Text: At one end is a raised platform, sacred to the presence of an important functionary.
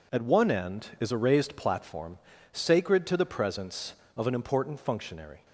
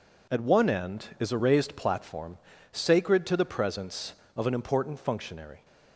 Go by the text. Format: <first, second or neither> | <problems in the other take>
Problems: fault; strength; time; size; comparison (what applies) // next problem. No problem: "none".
neither | none